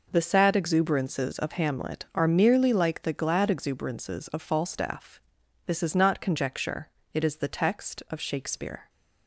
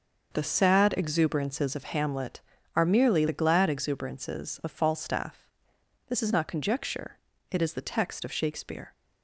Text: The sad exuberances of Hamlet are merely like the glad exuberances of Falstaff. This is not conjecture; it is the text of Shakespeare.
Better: first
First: none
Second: starts louder than the rest; until 1.3 s; 6 dB // skips "like"; at 3.2 s

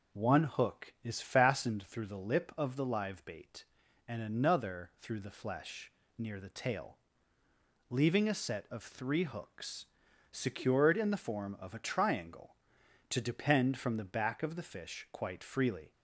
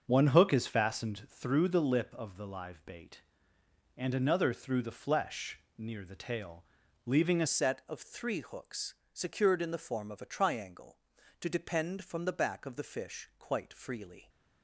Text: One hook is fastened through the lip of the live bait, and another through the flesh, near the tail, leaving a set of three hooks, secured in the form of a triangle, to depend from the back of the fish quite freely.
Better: first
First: none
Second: starts louder than the rest; until 1.0 s; 6.5 dB // changes voice at "set"; from 7.4 s on; 6.8 s long

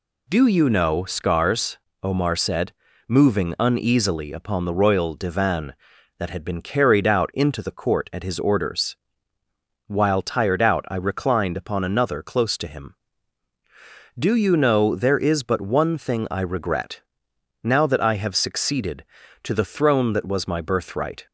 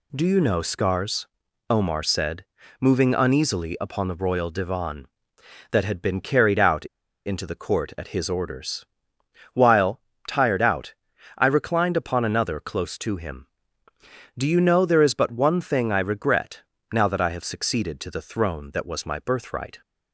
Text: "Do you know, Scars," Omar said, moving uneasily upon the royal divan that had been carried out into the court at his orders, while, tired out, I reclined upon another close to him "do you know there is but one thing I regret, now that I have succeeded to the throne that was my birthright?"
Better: first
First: none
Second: pauses between "out" and "into"; at 6.8 s; 0.40 s long

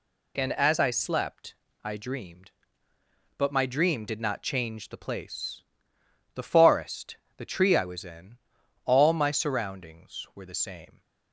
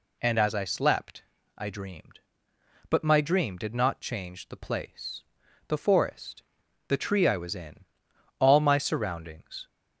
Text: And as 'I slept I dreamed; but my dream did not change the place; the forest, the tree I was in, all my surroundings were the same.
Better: first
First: pauses between "slept" and "I"; slight; at 1.5 s; 0.28 s long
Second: pauses between "slept" and "I"; slight; at 1.2 s; 0.34 s long // stops before "were the same"; at 9.6 s

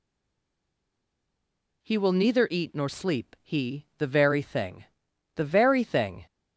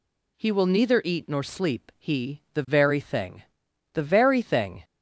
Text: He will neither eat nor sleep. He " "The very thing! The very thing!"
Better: second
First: stays silent before the first word; noticeable; until 1.8 s; 1.8 s long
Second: none

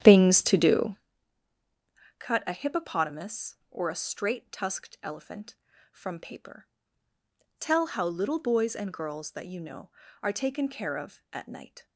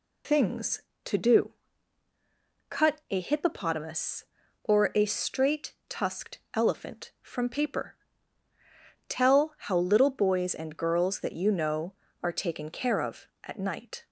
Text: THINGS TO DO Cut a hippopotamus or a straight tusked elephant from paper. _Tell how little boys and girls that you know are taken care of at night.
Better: second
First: starts louder than the rest; strong; until 1.1 s; 10 dB // pauses between "DO" and "Cut"; at 0.9 s; 1.2 s long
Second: pauses between "DO" and "Cut"; at 1.4 s; 1.1 s long

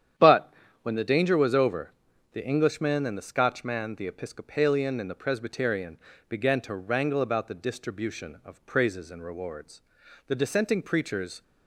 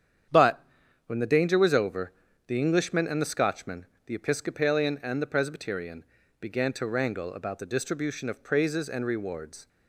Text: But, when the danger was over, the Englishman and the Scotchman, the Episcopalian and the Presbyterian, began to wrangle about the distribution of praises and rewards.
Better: second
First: starts louder than the rest; strong; until 1.4 s; 9.5 dB // goes on to say "The dissenting preachers"; noticeable; from 10.2 s on; 1.1 s long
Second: starts louder than the rest; strong; until 1.7 s; 9 dB

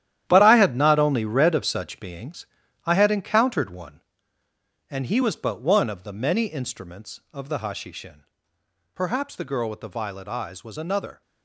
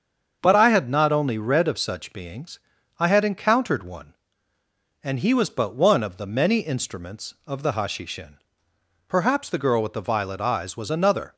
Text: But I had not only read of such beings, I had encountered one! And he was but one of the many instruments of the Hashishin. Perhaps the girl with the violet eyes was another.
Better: second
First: gets quieter; strong; throughout; 11 dB // starts louder than the rest; strong; until 1.2 s; 11.5 dB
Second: starts louder than the rest; until 1.4 s; 6.5 dB

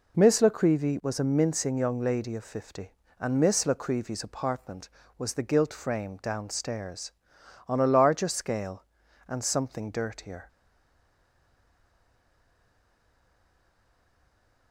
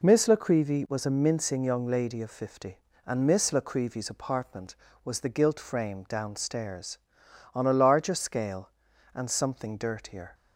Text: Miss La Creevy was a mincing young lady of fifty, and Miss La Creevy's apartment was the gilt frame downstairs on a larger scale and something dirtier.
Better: second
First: stays silent after the last word; strong; from 10.4 s on; 4.3 s long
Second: none

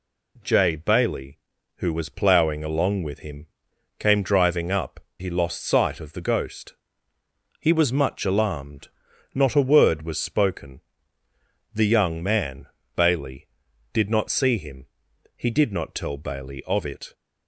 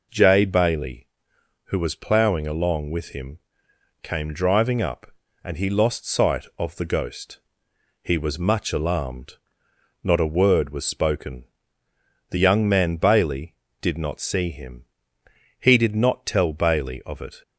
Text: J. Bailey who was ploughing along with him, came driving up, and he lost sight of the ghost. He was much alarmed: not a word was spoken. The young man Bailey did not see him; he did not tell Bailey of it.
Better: second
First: skips "and"; at 5.0 s // pauses between "man" and "Bailey"; slight; at 12.6 s; 0.30 s long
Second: none

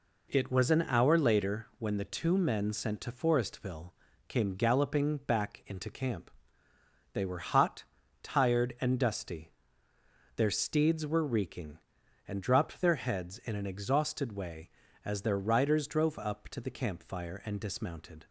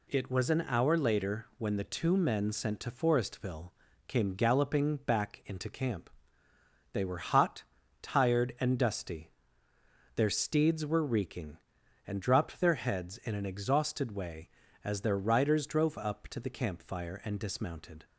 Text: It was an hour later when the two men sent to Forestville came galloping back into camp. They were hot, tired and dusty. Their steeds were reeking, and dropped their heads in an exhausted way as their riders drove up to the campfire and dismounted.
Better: second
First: starts louder than the rest; until 1.5 s; 4 dB // pauses between "Forestville" and "came"; at 3.8 s; 0.38 s long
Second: pauses between "Forestville" and "came"; at 3.6 s; 0.38 s long

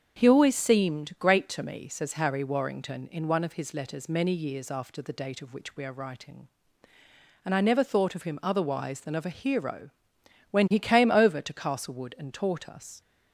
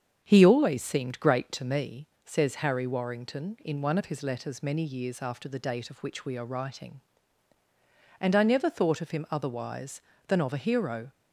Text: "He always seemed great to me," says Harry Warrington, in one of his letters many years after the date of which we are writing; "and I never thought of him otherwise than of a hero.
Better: second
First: starts louder than the rest; strong; until 1.2 s; 7 dB // goes on to say "When he came over to Castlewood and taught us"; strong; from 10.4 s on; 2.5 s long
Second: starts louder than the rest; strong; until 1.2 s; 7 dB

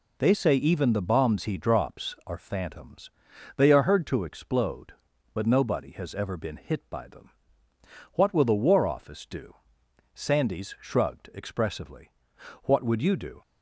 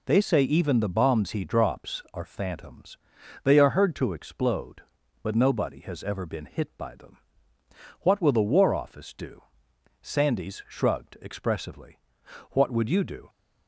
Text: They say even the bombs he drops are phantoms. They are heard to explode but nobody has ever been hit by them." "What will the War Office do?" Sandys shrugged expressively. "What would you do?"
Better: neither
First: none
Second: none

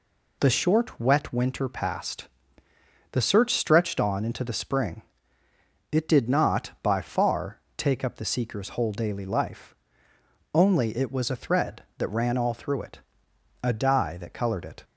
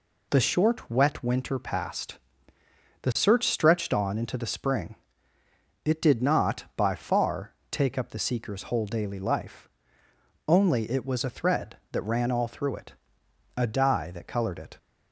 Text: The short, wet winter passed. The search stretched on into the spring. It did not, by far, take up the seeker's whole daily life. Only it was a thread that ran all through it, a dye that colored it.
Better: neither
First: none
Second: none

